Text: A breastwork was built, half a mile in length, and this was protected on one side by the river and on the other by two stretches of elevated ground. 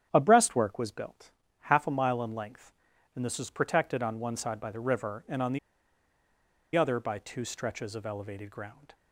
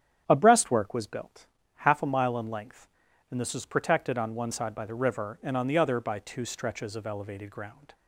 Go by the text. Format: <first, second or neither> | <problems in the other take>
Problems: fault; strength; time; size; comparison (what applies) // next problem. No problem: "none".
second | starts louder than the rest; strong; until 1.1 s; 9.5 dB; strong in the second // pauses between "the" and "other"; at 5.5 s; 1.1 s long